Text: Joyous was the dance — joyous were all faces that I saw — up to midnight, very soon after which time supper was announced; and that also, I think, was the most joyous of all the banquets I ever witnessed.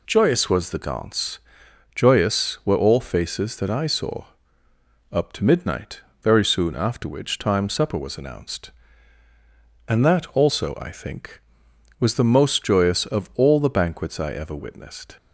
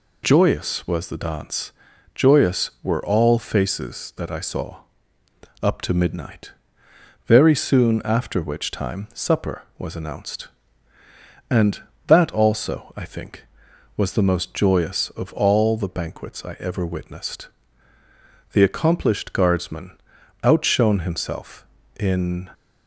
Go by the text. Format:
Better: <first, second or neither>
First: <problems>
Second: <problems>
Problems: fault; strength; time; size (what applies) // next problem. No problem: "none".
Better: first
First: none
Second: goes on to say "The accomplished guardsman outshone himself in"; strong; from 18.5 s on; 3.9 s long